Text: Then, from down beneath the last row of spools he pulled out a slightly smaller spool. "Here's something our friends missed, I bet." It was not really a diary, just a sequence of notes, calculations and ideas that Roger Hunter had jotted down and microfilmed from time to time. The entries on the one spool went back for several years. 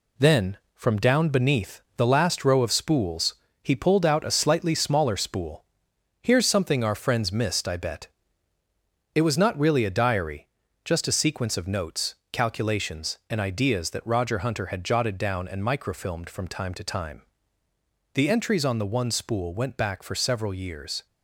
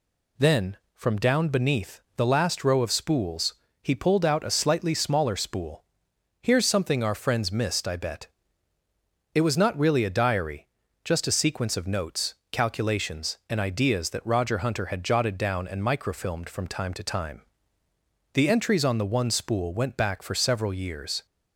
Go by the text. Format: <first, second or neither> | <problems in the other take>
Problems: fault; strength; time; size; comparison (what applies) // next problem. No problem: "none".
second | gets quieter; noticeable; throughout; 5.5 dB // pauses between "beneath" and "the"; slight; at 1.8 s; 0.16 s long; slight in the second // pauses between "spools" and "he"; slight; at 3.3 s; 0.28 s long; slight in the second